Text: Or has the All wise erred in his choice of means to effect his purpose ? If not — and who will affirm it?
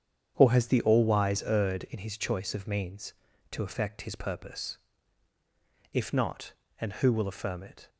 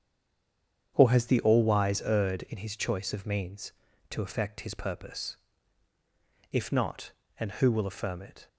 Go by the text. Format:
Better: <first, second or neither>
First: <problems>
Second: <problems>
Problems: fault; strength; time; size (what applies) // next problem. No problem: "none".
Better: first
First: starts louder than the rest; strong; until 1.3 s; 8 dB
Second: stays silent before the first word; slight; until 0.9 s; 0.9 s long // starts louder than the rest; strong; until 1.9 s; 8 dB